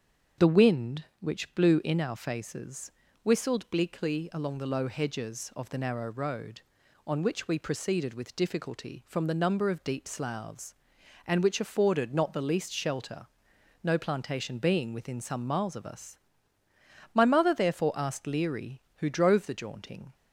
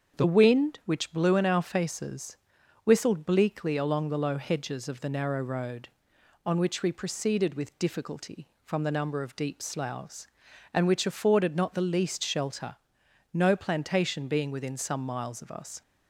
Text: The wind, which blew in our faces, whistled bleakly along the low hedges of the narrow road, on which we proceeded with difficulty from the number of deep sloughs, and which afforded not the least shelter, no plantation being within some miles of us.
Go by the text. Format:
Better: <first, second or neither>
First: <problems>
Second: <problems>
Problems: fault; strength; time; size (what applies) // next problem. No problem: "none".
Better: second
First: starts louder than the rest; strong; until 1.5 s; 7.5 dB // goes on to say "My mother therefore asked Leary who drove the jaunting"; strong; from 17.1 s on; 3.0 s long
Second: starts louder than the rest; until 1.2 s; 7 dB